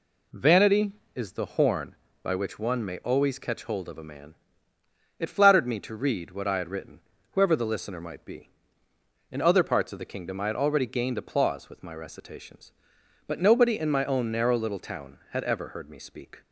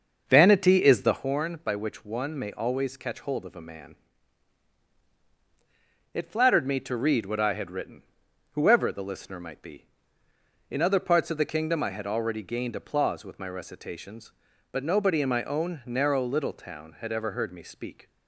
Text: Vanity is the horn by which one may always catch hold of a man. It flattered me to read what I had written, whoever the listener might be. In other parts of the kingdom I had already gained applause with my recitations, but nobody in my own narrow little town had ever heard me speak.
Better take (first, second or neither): first